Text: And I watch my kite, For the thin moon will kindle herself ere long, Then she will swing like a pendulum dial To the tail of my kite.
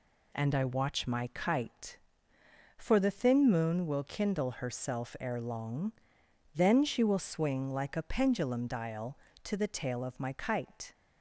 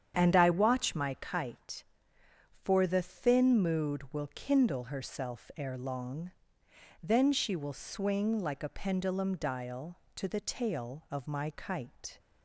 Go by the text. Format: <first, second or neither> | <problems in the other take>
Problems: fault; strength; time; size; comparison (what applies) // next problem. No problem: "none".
first | starts louder than the rest; strong; until 1.1 s; 8.5 dB // says "mood" for "moon"; at 3.6 s